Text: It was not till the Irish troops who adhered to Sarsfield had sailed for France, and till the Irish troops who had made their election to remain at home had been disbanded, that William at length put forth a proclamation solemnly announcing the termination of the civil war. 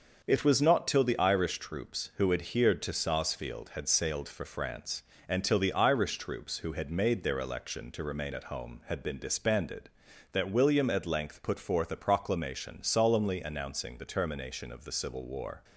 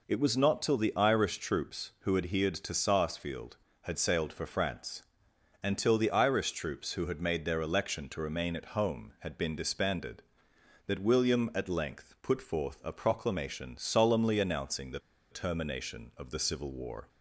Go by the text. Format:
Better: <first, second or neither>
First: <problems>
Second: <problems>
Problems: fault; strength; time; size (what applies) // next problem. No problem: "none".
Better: first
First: none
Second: pauses between "the" and "termination"; slight; at 14.9 s; 0.33 s long